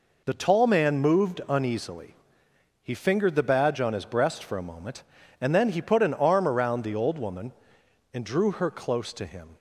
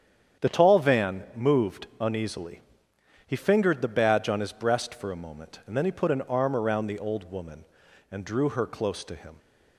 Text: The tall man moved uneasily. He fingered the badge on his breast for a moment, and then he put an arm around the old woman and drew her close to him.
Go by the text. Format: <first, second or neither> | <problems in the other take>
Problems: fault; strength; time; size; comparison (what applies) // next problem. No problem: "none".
first | starts louder than the rest; strong; until 1.4 s; 8.5 dB // says "van" for "man"; at 0.7 s